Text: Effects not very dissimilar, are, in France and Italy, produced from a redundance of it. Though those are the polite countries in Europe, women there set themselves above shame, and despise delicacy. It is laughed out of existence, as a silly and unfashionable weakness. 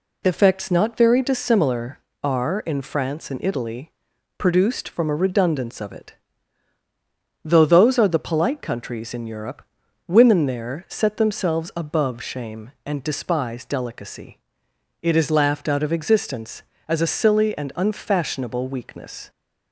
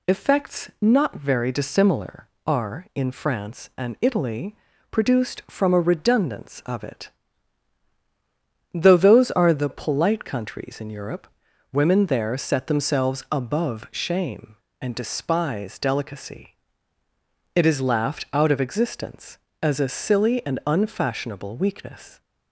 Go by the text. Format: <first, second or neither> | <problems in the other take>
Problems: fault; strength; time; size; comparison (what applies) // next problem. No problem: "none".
neither | none